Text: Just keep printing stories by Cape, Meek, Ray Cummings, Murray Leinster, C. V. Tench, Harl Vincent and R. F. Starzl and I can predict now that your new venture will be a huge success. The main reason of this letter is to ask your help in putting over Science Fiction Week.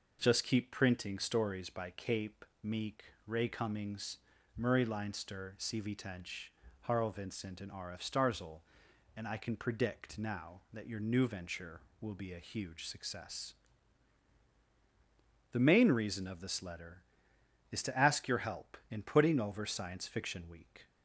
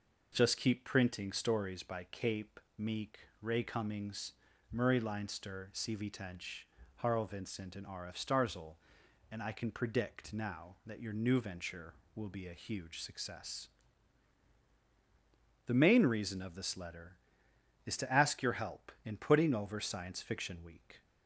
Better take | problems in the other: neither | none

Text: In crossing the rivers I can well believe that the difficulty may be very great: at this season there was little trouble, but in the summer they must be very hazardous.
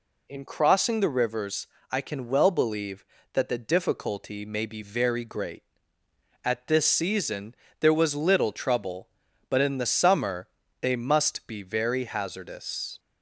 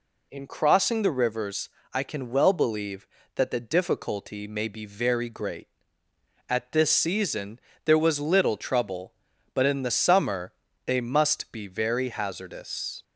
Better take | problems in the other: neither | pauses between "rivers" and "I"; slight; the same in both // pauses between "season" and "there"; slight; the same in both // pauses between "summer" and "they"; slight; the same in both

